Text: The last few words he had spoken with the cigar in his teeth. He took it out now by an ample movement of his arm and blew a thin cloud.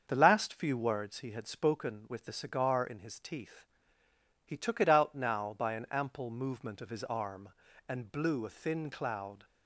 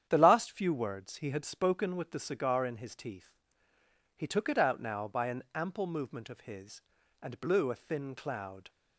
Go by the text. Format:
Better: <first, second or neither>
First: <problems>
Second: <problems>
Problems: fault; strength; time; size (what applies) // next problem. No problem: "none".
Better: first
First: starts louder than the rest; until 1.1 s; 7 dB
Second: starts louder than the rest; strong; until 1.1 s; 9.5 dB // skips "arm"; at 7.0 s